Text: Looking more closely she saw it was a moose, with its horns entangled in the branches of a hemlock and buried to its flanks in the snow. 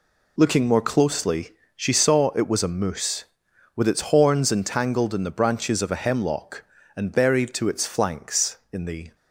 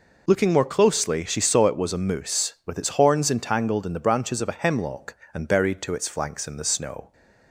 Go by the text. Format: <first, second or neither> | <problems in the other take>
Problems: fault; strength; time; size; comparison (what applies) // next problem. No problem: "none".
second | pauses between "closely" and "she"; slight; at 1.5 s; 0.24 s long // stops before "snow"; at 9.1 s